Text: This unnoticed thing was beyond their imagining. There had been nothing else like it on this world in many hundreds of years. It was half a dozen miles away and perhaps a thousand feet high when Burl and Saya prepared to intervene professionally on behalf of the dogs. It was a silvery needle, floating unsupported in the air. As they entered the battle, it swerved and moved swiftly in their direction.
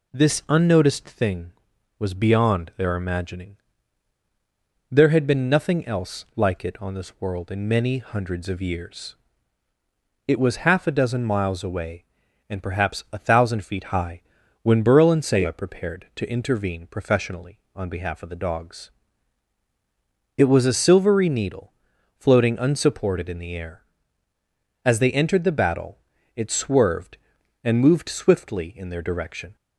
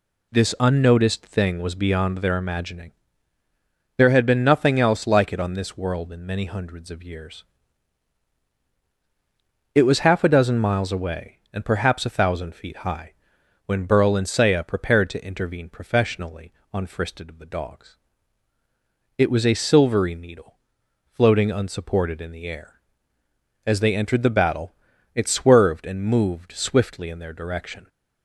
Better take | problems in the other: first | pauses between "high" and "when"; noticeable; at 13.1 s; 0.52 s long; also in the first // says "fristed" for "behalf"; at 16.8 s

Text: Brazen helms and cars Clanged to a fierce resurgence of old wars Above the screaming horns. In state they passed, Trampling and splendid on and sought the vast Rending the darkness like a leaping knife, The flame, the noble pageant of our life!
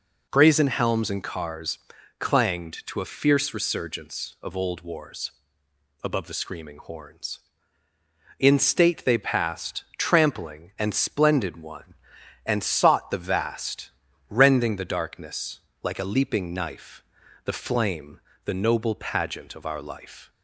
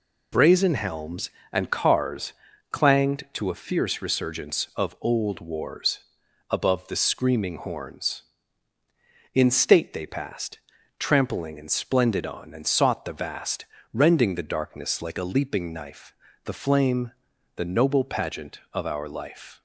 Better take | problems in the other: second | pauses between "cars" and "Clanged"; at 1.7 s; 0.42 s long; also in the second // pauses between "wars" and "Above"; noticeable; at 5.3 s; 0.72 s long; noticeable in the second // says "one" for "on"; at 11.5 s // pauses between "vast" and "Rending"; at 13.8 s; 0.40 s long; slight in the second // pauses between "darkness" and "like"; slight; at 15.5 s; 0.22 s long

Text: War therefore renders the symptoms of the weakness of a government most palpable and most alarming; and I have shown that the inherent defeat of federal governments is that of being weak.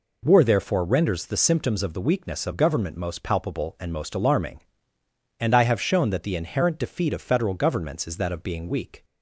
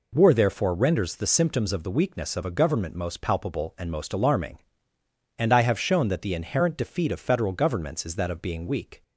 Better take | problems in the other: second | skips "a"; at 2.5 s

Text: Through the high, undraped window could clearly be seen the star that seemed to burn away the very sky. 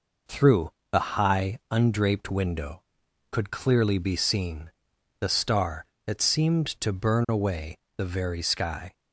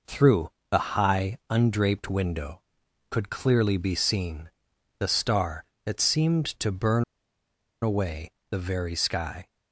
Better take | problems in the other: first | pauses between "Through" and "the"; slight; at 0.5 s; 0.20 s long; slight in the first // pauses between "seen" and "the"; noticeable; at 4.5 s; 0.48 s long; noticeable in the first // pauses between "burn" and "away"; noticeable; at 7.0 s; 0.78 s long // pauses between "away" and "the"; slight; at 8.3 s; 0.20 s long; slight in the first

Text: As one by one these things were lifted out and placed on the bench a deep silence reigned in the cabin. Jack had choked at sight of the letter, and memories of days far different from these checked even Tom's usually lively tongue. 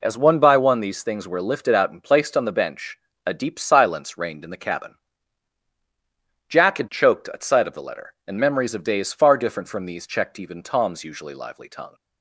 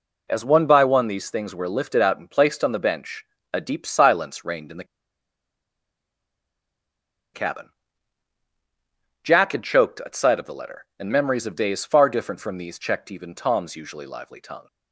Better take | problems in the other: first | pauses between "bench" and "a"; slight; at 3.2 s; 0.30 s long; slight in the first // pauses between "the" and "cabin"; strong; at 4.8 s; 2.5 s long

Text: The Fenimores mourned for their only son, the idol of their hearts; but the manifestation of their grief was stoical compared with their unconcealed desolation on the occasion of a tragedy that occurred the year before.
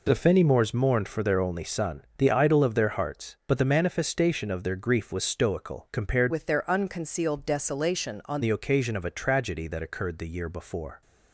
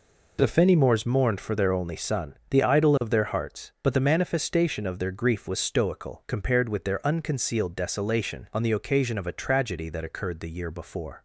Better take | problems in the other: second | changes voice from "with" to "on"; from 6.3 to 8.4 s; 2.1 s long

